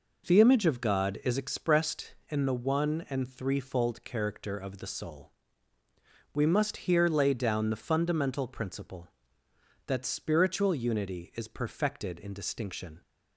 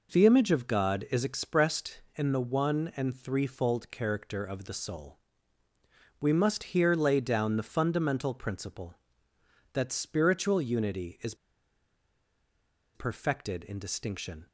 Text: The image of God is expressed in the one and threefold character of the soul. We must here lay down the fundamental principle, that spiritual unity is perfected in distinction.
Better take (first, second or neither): first